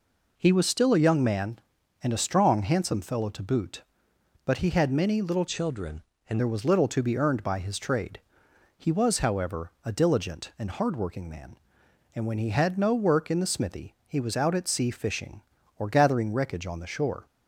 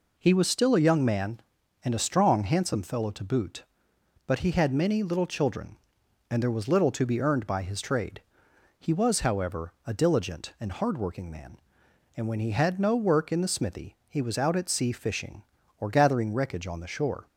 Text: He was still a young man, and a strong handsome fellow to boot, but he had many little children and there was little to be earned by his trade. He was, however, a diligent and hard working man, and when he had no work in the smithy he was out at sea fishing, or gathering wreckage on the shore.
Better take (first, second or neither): second